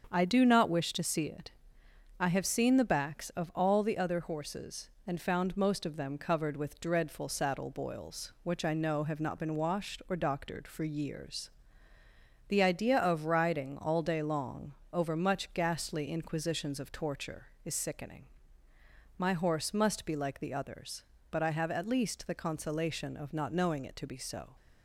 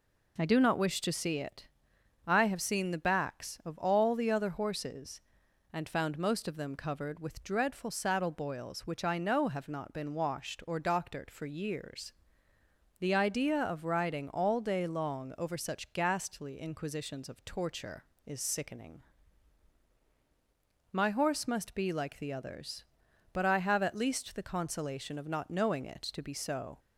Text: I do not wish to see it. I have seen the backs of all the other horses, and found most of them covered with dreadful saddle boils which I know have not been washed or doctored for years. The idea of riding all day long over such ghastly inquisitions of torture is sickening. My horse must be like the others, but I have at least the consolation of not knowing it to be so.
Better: second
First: starts louder than the rest; until 1.1 s; 7 dB // pauses between "long" and "over"; slight; at 14.7 s; 0.20 s long // says "much" for "such"; at 15.1 s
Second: none

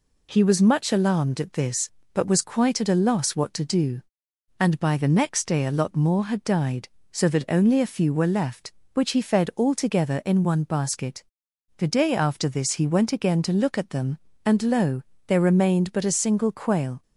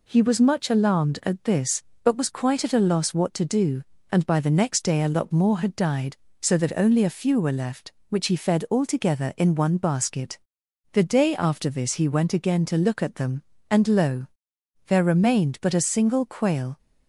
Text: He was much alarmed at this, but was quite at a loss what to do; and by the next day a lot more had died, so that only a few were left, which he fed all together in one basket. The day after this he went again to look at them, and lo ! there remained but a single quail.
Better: neither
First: none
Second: none

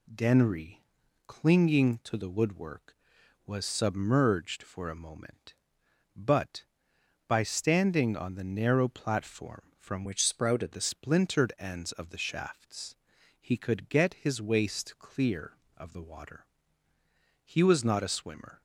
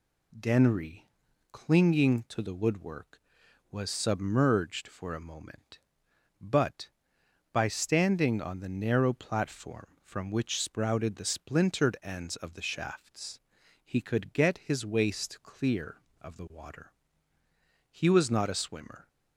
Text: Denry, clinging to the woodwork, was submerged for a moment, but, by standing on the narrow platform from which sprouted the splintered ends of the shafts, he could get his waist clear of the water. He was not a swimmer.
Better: second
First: changes voice from "which" to "sprouted"; from 10.0 to 10.7 s; 0.7 s long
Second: none

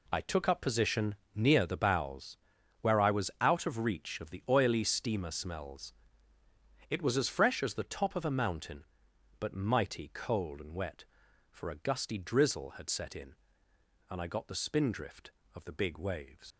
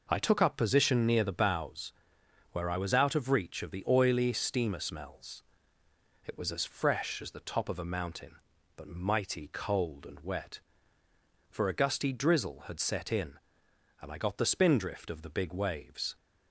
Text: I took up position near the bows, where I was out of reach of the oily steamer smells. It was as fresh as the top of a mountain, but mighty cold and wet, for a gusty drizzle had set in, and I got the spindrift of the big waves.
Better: second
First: pauses between "position" and "near"; slight; at 1.1 s; 0.20 s long // leaves "waves" unfinished; at 16.5 s; 105 ms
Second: none

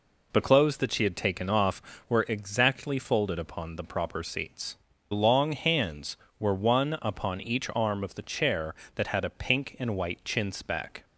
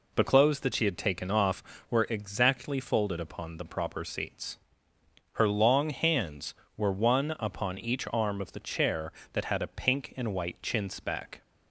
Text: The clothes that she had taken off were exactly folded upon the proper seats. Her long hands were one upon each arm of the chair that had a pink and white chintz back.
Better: second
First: skips "Her"; at 4.9 s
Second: none

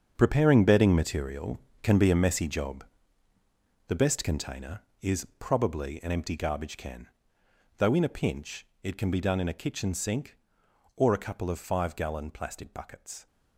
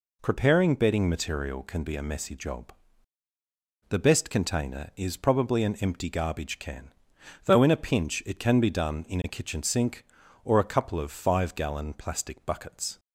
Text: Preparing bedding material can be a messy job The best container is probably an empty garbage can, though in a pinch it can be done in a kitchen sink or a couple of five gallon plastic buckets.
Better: second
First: gets quieter; strong; throughout; 12.5 dB // pauses between "job" and "The"; at 2.8 s; 1.0 s long // pauses between "pinch" and "it"; slight; at 8.6 s; 0.19 s long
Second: pauses between "job" and "The"; at 2.7 s; 1.1 s long

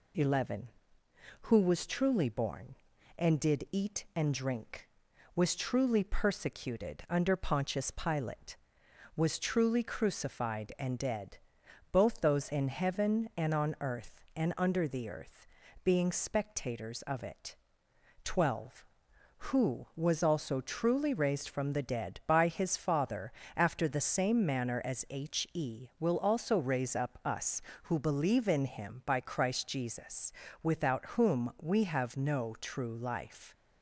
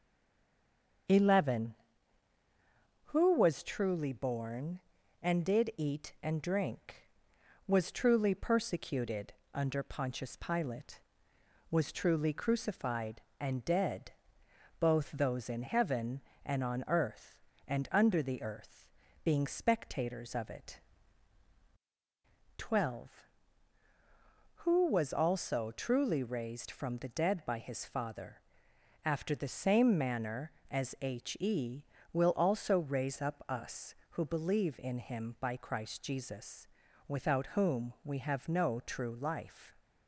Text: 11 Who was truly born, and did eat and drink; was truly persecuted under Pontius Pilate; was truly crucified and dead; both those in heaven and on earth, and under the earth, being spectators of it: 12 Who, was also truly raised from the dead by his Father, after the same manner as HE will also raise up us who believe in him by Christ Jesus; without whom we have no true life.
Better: first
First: none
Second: stays silent before the first word; until 1.0 s; 1.0 s long // starts louder than the rest; until 3.4 s; 7 dB // pauses between "persecuted" and "under"; slight; at 9.3 s; 0.20 s long

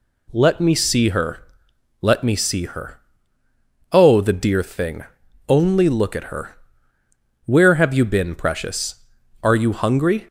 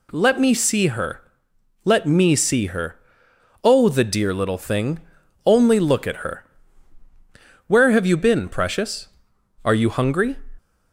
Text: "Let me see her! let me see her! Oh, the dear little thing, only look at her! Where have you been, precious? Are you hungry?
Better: second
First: skips "little"; at 4.6 s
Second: none

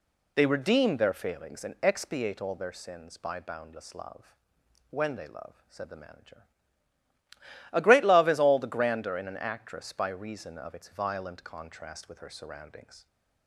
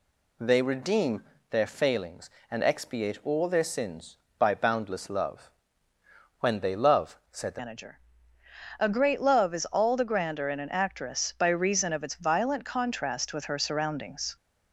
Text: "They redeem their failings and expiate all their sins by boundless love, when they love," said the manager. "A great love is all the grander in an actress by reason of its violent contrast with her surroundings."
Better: first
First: none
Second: pauses between "redeem" and "their"; slight; at 1.2 s; 0.26 s long // changes voice at "manager"; from 7.5 s on; 6.8 s long

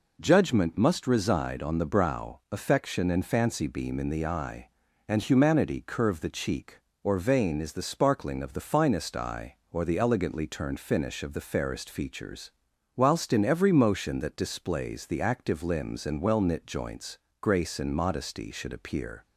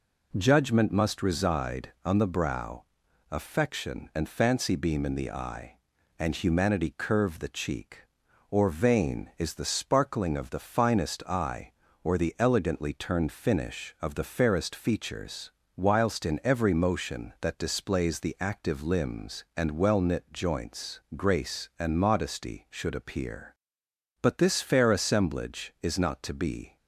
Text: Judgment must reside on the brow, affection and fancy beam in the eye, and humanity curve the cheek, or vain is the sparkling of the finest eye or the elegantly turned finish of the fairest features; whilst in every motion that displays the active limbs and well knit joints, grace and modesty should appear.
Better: first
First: none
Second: goes on to say "But this fair assemblage is not to be"; strong; from 24.2 s on; 2.5 s long

